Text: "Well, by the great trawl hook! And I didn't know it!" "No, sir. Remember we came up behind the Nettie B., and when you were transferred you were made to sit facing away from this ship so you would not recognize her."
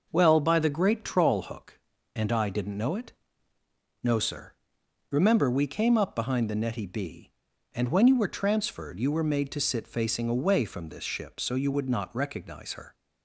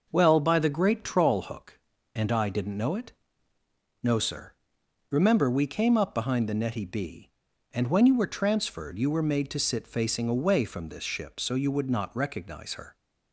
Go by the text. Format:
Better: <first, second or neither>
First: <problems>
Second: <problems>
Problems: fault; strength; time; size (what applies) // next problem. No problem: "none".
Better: neither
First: none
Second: none